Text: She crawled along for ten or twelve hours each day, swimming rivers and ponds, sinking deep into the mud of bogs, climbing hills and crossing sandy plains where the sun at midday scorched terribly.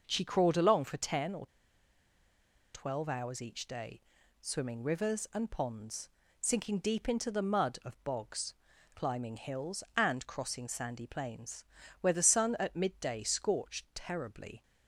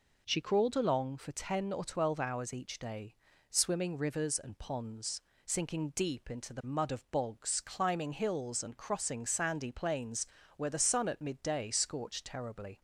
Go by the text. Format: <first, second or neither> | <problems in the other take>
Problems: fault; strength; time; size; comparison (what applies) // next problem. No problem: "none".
second | starts louder than the rest; noticeable; until 1.0 s; 6 dB // pauses between "or" and "twelve"; strong; at 1.4 s; 1.2 s long // pauses between "plains" and "where"; at 11.6 s; 0.38 s long; slight in the second